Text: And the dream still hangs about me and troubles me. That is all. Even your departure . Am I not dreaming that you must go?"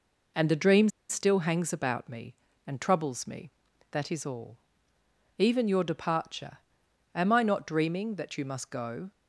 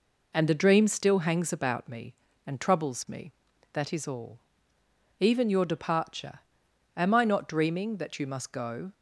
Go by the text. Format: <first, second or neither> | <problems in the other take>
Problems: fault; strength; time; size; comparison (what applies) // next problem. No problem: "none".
second | pauses between "dream" and "still"; slight; at 0.8 s; 0.21 s long